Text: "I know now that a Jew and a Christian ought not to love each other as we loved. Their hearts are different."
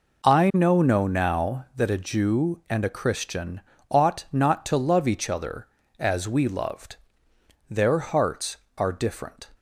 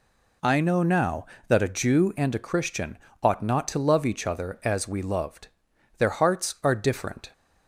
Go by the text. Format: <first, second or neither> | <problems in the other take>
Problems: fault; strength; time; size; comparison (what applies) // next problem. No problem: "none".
second | says "know" twice; at 0.8 s // pauses between "Christian" and "ought"; slight; at 3.6 s; 0.30 s long; slight in the second